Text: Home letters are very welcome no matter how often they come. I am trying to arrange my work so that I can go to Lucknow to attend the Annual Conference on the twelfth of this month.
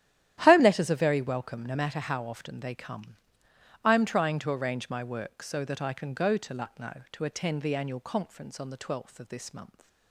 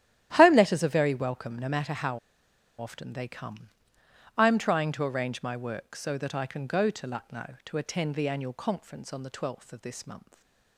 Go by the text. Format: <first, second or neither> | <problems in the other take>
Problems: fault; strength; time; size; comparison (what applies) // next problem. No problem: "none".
first | starts louder than the rest; strong; until 1.3 s; 12 dB; strong in the first // pauses between "how" and "often"; noticeable; at 2.1 s; 0.61 s long // stays silent after the last word; slight; from 10.2 s on; 0.5 s long